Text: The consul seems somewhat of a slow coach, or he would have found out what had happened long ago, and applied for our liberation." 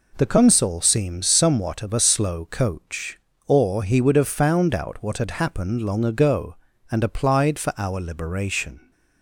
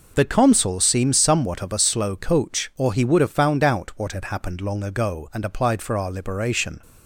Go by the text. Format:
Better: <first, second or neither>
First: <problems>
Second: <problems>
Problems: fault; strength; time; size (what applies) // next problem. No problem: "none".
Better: neither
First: none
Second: none